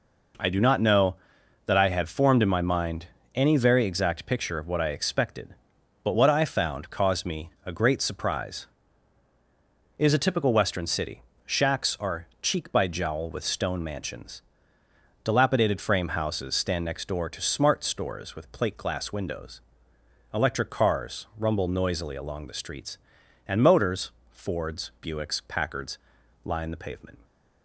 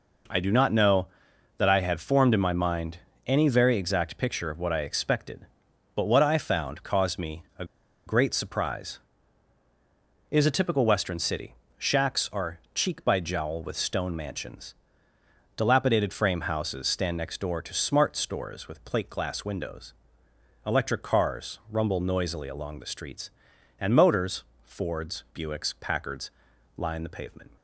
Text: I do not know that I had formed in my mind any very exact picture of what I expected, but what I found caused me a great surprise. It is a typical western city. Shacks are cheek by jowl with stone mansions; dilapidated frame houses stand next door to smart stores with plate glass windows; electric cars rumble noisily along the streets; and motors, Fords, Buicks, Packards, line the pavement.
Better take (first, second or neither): first